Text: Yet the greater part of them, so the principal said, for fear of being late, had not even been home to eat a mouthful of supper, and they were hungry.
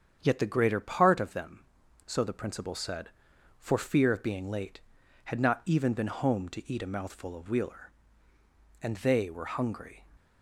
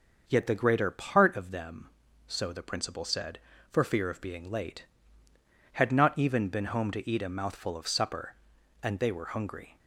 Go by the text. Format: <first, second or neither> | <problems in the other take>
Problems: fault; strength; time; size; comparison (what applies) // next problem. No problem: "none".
second | starts louder than the rest; strong; until 1.2 s; 8 dB; also in the second // says "wheeler" for "supper"; at 7.4 s